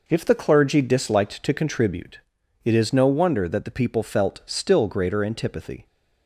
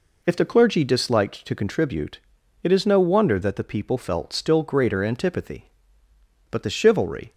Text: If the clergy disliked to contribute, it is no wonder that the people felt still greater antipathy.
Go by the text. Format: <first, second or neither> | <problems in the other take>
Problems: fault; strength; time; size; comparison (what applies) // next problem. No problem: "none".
first | goes on to say "But the chivalry"; noticeable; from 6.5 s on; 0.82 s long